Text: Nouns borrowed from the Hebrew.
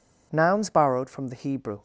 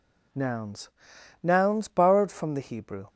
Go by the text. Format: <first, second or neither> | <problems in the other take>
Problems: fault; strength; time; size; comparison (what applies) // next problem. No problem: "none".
first | says "Nouns" twice; at 1.4 s